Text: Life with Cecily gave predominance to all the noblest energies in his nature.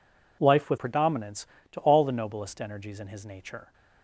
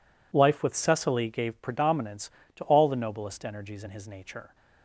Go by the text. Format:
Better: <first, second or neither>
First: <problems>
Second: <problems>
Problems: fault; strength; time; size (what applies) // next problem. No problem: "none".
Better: second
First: skips "Cecily gave"; at 0.7 s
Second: none